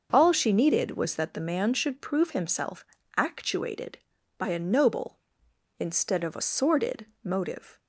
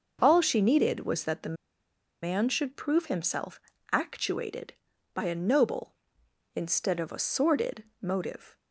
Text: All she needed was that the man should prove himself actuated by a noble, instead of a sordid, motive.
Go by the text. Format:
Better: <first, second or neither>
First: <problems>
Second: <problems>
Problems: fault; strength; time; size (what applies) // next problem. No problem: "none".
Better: first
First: pauses between "himself" and "actuated"; slight; at 2.8 s; 0.34 s long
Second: pauses between "the" and "man"; noticeable; at 1.5 s; 0.66 s long // pauses between "himself" and "actuated"; slight; at 3.5 s; 0.34 s long